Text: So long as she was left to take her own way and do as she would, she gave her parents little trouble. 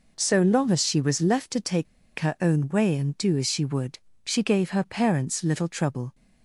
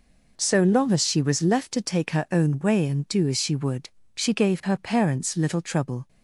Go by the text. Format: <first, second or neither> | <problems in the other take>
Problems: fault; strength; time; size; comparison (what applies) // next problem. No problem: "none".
second | pauses between "take" and "her"; slight; at 1.8 s; 0.33 s long